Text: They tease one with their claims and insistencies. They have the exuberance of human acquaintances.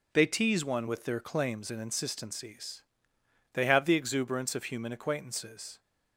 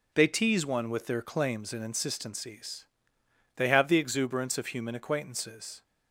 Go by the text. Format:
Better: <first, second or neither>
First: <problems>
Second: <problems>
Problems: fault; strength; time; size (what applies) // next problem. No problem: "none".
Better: neither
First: none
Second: none